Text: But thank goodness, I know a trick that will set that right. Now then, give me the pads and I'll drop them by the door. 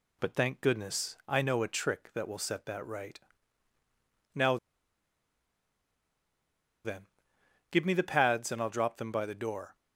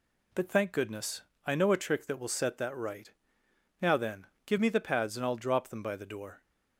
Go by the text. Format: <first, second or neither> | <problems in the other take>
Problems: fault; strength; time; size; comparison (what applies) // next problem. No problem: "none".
second | pauses between "Now" and "then"; strong; at 4.5 s; 2.2 s long